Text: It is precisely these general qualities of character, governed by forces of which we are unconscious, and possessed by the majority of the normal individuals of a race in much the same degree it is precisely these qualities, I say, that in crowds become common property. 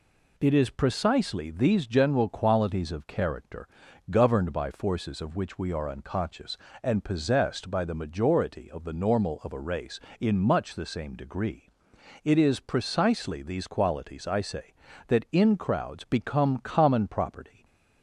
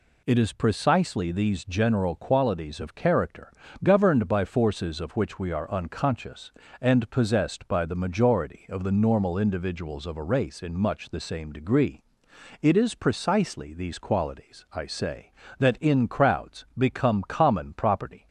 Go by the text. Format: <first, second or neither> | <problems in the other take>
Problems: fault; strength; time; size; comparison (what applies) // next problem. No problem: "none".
second | skips "individuals"; at 9.4 s // pauses between "degree" and "it"; noticeable; at 11.6 s; 0.54 s long; noticeable in the second